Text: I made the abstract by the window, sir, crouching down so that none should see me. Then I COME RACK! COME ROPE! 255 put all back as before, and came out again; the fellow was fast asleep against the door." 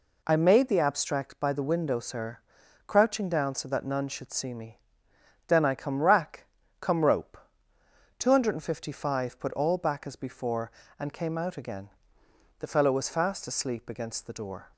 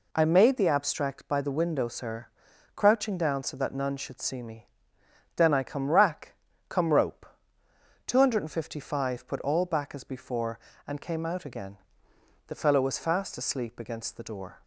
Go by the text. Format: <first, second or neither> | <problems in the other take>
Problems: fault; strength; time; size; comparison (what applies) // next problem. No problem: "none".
neither | none